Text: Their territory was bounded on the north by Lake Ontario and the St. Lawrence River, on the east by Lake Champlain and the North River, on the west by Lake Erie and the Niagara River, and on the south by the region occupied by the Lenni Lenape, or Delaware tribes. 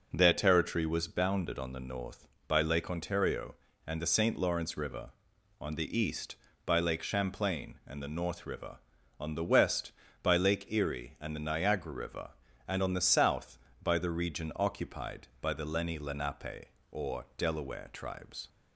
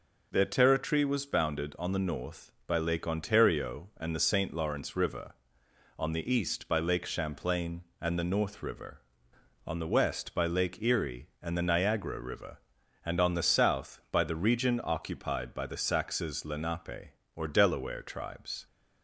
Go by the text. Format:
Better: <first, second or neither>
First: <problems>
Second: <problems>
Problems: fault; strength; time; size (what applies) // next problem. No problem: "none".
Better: first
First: none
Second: says "Saxes" for "Lenni"; at 15.7 s